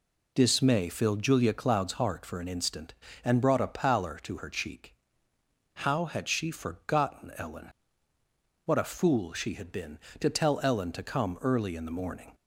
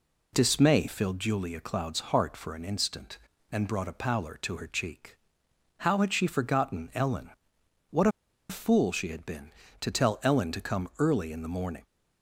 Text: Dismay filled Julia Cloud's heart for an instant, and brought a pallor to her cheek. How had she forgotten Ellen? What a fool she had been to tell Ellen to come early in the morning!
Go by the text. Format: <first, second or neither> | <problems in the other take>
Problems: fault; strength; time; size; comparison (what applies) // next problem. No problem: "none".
first | pauses between "What" and "a"; at 8.0 s; 0.41 s long